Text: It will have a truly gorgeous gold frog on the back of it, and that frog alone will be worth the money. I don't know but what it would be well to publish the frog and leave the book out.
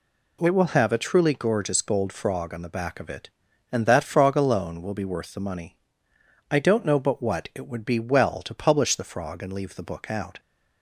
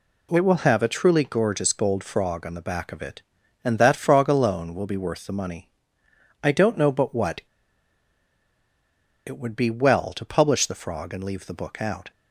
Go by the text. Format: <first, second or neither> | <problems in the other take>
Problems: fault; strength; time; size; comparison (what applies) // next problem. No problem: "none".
first | pauses between "what" and "it"; strong; at 7.4 s; 1.8 s long